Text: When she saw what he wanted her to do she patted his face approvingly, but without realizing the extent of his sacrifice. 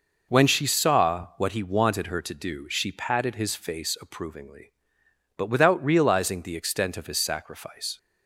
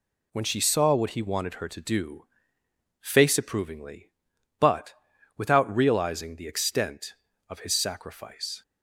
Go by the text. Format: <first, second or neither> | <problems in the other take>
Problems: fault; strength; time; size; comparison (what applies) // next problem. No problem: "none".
first | skips "she patted his"; at 2.6 s // pauses between "but" and "without"; at 4.9 s; 0.44 s long